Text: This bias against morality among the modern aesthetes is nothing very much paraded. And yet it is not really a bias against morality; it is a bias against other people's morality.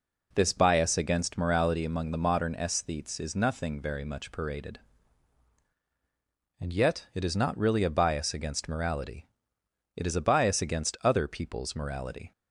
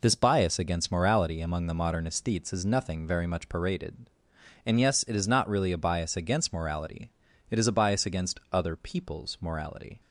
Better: first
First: none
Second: says "yes" for "yet"; at 4.8 s

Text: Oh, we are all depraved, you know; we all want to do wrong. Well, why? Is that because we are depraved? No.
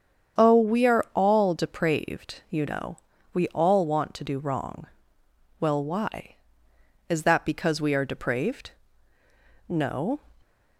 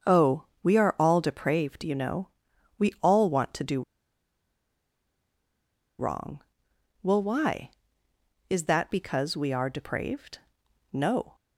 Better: first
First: starts louder than the rest; strong; until 1.4 s; 8 dB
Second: starts louder than the rest; until 1.2 s; 7 dB // pauses between "do" and "wrong"; strong; at 3.8 s; 2.1 s long

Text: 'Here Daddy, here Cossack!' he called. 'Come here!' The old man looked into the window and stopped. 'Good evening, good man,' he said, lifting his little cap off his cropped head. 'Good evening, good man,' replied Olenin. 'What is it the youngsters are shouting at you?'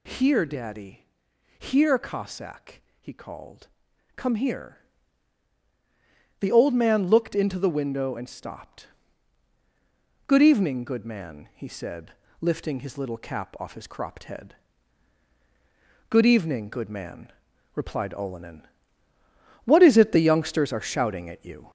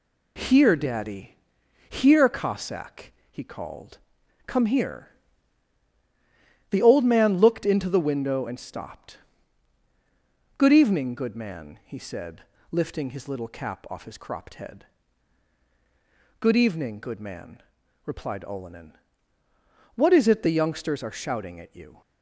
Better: second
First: gets louder; slight; throughout; 2.5 dB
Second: none

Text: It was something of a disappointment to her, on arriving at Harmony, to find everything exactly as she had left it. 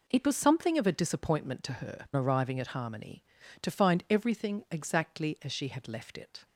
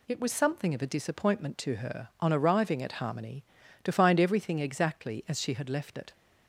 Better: second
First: skips "on"; at 2.1 s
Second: none

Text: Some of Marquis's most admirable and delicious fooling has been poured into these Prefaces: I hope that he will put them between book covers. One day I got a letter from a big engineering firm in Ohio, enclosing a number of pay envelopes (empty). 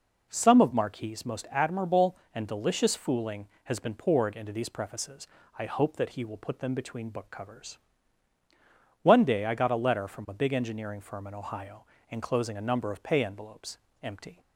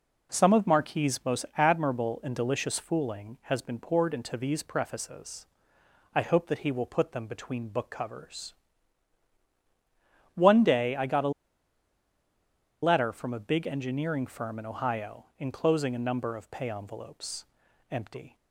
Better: first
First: none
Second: pauses between "a" and "letter"; strong; at 11.3 s; 1.5 s long

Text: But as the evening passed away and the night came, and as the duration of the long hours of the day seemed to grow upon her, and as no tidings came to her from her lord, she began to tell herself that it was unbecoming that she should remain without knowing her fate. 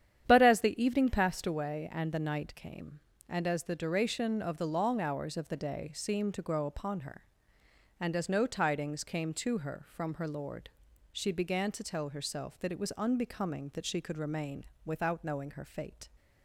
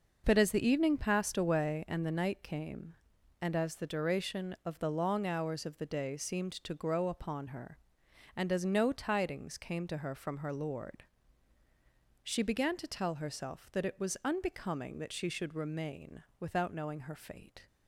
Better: second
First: starts louder than the rest; strong; until 1.2 s; 9.5 dB // says "could" for "should"; at 14.0 s // pauses between "remain" and "without"; slight; at 14.6 s; 0.22 s long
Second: pauses between "remain" and "without"; slight; at 16.2 s; 0.18 s long

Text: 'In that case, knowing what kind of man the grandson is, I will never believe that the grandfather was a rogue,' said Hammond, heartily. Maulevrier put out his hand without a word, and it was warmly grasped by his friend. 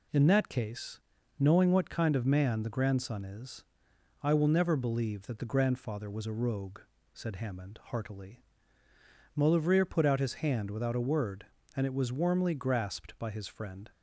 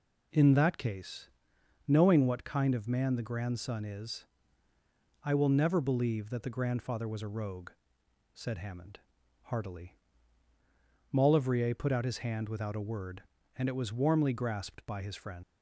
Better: first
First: none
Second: leaves "friend" unfinished; at 15.4 s; 105 ms

